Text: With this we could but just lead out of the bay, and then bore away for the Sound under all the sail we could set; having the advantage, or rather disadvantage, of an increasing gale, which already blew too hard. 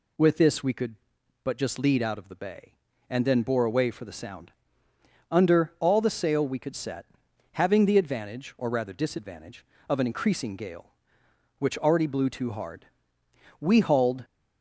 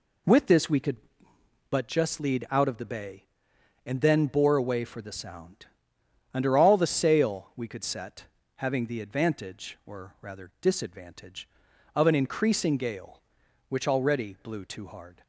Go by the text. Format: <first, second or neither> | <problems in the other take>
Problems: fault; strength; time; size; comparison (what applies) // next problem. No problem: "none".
second | pauses between "Sound" and "under"; noticeable; at 4.5 s; 0.76 s long; noticeable in the second // goes on to say "We hauled"; noticeable; from 13.6 s on; 0.64 s long